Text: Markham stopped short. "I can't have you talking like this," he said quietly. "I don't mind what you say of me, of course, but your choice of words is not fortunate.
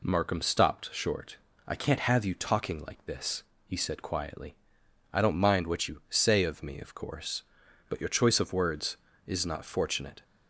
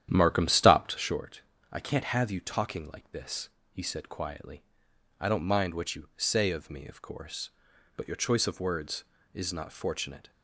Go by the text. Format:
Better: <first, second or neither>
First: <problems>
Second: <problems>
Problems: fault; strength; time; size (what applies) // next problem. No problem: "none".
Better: first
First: none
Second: starts louder than the rest; strong; until 1.2 s; 10.5 dB